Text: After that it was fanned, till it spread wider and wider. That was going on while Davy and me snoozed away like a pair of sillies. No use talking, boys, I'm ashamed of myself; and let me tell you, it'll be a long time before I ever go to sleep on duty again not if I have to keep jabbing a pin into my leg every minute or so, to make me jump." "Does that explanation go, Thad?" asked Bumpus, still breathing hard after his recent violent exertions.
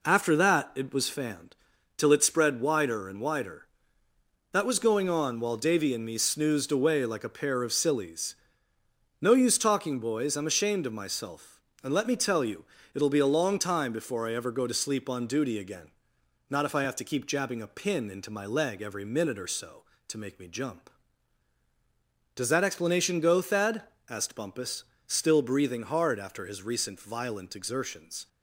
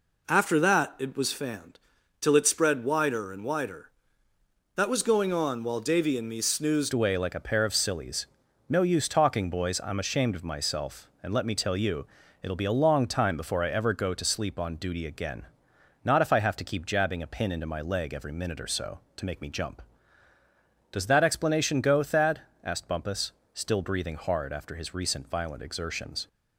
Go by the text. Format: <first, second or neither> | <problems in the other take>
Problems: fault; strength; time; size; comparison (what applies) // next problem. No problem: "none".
first | changes voice at "away"; from 6.9 s on; 19.3 s long // pauses between "again" and "not"; noticeable; at 15.4 s; 0.60 s long; noticeable in the first